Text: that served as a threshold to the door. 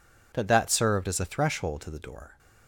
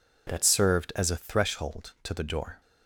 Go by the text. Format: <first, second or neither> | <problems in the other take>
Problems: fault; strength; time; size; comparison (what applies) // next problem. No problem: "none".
second | says "that" twice; at 0.4 s